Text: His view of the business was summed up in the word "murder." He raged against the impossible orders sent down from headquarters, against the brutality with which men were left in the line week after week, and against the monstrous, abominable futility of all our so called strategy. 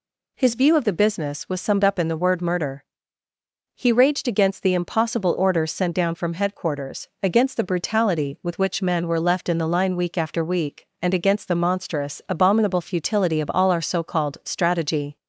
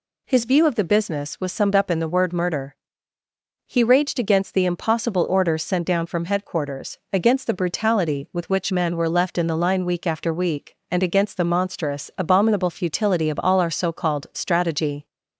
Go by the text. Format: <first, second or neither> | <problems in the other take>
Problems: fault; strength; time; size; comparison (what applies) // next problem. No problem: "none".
neither | none